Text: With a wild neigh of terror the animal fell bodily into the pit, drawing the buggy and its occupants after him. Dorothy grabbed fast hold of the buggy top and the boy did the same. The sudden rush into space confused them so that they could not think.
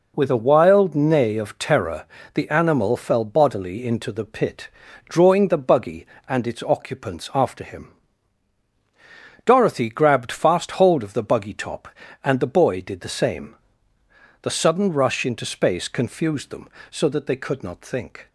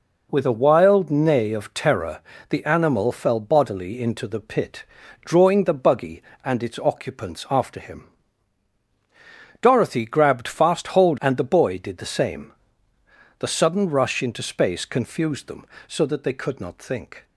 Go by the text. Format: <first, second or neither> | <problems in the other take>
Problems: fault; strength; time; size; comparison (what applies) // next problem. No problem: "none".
first | pauses between "terror" and "the"; slight; at 2.2 s; 0.30 s long; slight in the first // skips "of the buggy top"; at 11.1 s